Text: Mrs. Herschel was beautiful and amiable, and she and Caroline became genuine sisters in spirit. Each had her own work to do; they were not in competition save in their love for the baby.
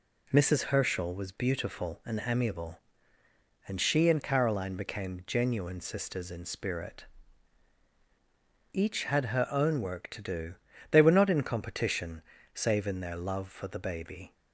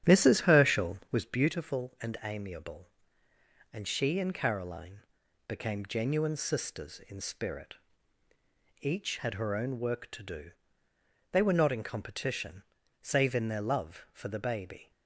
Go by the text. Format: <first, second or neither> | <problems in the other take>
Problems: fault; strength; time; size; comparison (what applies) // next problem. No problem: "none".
first | starts louder than the rest; strong; until 1.3 s; 10 dB // pauses between "Caroline" and "became"; noticeable; at 4.9 s; 0.48 s long // pauses between "competition" and "save"; at 12.6 s; 0.38 s long; slight in the first